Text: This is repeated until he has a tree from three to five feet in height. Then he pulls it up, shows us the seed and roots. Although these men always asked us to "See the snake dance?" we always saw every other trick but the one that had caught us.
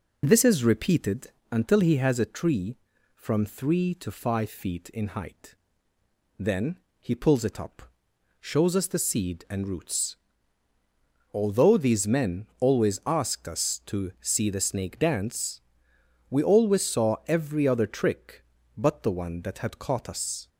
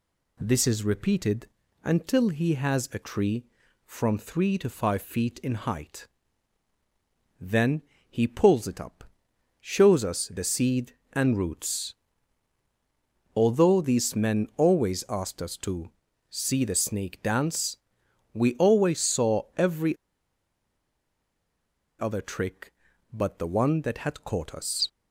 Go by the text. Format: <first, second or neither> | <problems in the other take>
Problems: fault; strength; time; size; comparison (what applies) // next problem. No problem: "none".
first | pauses between "repeated" and "until"; slight; at 1.4 s; 0.36 s long; slight in the first // pauses between "Then" and "he"; slight; at 7.8 s; 0.28 s long; slight in the first // pauses between "to" and "See"; at 15.8 s; 0.40 s long // pauses between "saw" and "every"; slight; at 19.4 s; 0.16 s long // pauses between "every" and "other"; strong; at 19.9 s; 2.0 s long